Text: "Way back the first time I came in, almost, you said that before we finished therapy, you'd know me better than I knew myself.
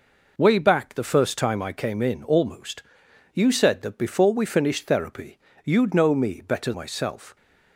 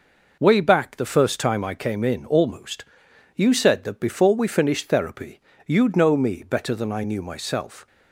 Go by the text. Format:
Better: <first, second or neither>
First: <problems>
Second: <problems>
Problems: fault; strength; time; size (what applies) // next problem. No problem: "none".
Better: second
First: skips "than I knew"; at 6.7 s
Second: none